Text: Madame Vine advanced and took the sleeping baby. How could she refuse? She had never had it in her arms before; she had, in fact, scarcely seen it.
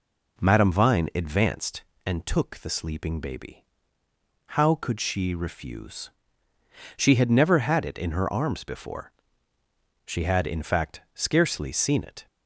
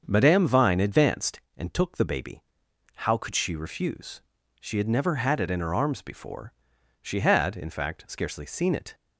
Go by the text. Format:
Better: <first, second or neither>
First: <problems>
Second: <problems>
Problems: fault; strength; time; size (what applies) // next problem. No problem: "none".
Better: first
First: none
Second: starts louder than the rest; until 1.0 s; 7 dB // skips "sleeping"; at 2.0 s